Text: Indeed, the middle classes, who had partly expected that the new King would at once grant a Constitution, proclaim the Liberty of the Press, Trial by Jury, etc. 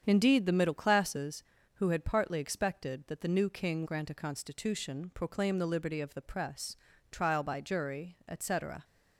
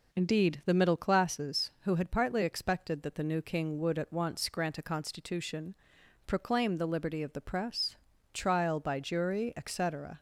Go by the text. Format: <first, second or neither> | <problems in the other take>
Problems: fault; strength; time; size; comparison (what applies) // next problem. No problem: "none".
second | starts louder than the rest; strong; until 1.0 s; 8 dB // skips "would at once"; at 3.8 s